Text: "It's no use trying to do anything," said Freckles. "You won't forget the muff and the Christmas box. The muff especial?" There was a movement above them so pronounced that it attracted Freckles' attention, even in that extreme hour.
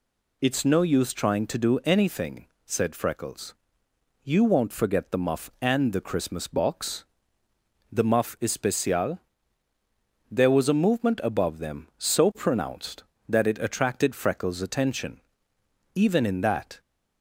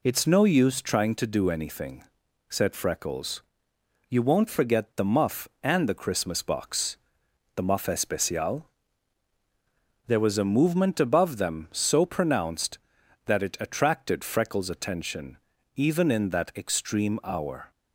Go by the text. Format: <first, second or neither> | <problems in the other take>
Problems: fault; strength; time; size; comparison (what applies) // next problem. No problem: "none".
second | stops before "extreme hour"; at 16.7 s